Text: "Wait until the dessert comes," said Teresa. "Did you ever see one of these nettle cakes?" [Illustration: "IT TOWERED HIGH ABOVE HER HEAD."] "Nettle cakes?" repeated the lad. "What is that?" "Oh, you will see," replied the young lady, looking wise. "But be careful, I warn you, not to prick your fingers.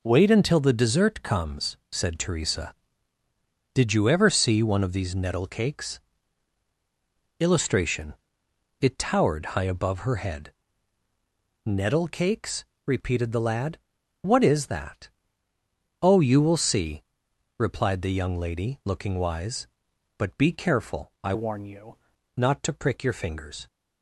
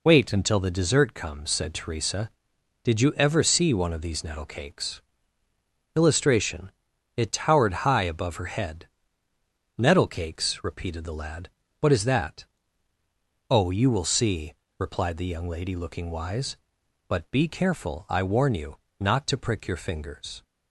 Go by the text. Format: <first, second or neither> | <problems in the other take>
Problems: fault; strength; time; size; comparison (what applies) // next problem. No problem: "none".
second | changes voice from "warn" to "you"; from 21.3 to 21.9 s; 0.6 s long